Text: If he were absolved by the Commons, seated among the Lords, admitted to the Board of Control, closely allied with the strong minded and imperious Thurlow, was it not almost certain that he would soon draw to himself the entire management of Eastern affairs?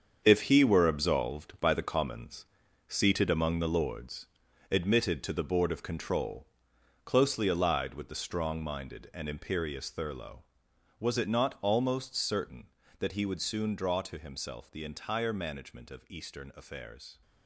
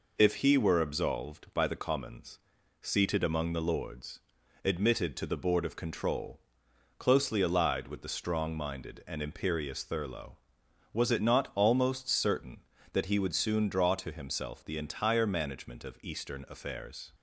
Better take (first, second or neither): second